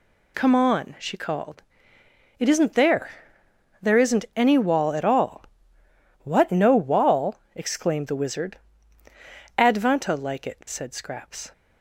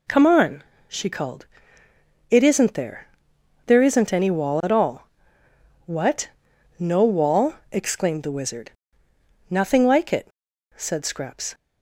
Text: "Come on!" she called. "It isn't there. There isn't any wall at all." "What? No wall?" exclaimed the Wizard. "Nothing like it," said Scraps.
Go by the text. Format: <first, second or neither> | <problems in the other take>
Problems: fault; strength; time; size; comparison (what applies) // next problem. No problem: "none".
second | says "Advanta" for "Nothing"; at 9.5 s